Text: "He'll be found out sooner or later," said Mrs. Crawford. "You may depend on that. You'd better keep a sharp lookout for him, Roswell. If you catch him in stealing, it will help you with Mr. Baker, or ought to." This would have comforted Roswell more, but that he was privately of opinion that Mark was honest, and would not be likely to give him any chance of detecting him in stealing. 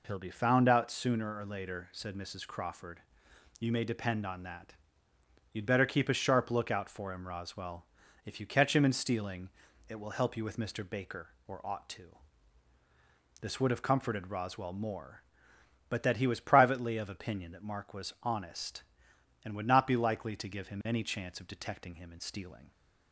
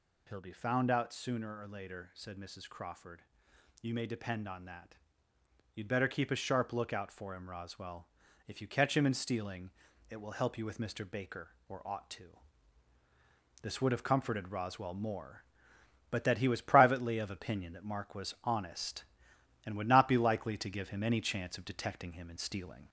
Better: first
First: none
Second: gets louder; slight; throughout; 2 dB

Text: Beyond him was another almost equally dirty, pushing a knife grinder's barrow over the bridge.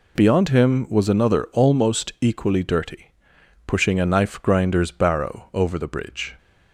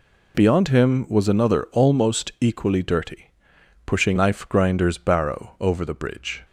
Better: first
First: none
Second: skips "a"; at 4.1 s

